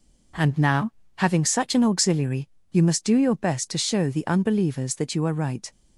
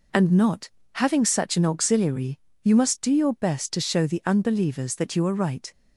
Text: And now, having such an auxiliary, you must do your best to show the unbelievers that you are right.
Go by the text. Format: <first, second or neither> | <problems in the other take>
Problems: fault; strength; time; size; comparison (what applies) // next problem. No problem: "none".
first | says "not" for "now"; at 0.3 s